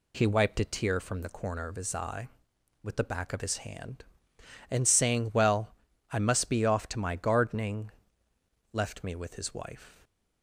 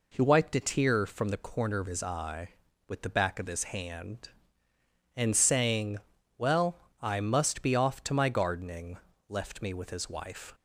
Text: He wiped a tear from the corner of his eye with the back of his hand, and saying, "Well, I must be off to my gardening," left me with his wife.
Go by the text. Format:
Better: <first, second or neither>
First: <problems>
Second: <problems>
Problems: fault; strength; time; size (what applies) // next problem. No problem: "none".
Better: neither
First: none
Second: none